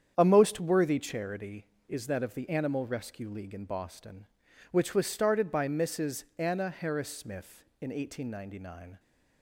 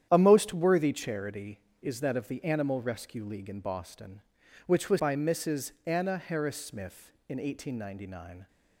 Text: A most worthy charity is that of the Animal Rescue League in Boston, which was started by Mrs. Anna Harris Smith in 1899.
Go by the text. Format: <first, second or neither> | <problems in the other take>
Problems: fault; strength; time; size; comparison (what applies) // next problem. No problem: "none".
first | starts louder than the rest; strong; until 1.1 s; 10 dB; strong in the first // skips "started"; at 4.9 s